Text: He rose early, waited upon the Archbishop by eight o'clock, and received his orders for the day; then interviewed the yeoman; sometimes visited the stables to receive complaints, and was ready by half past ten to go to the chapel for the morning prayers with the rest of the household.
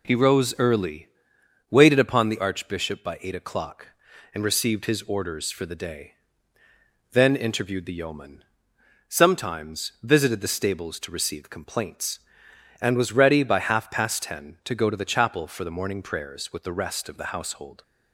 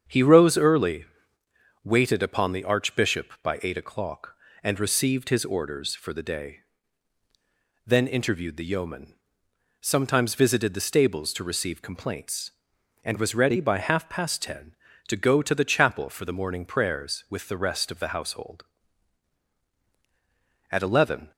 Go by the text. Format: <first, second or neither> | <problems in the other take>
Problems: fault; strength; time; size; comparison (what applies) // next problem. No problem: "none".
first | starts louder than the rest; strong; until 1.8 s; 7.5 dB // goes on to say "At eleven"; from 20.7 s on; 0.60 s long